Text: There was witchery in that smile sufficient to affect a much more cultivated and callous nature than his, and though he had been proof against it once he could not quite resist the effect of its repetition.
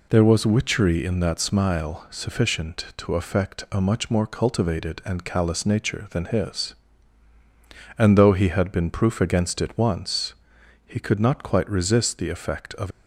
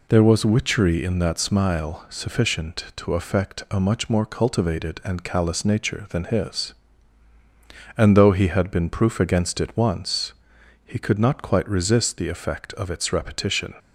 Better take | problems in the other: second | pauses between "once" and "he"; noticeable; at 10.3 s; 0.52 s long; noticeable in the second // stops before "its repetition"; at 12.9 s

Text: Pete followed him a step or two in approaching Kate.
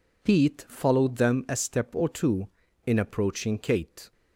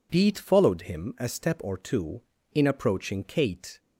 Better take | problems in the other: second | says "them" for "him"; at 1.1 s

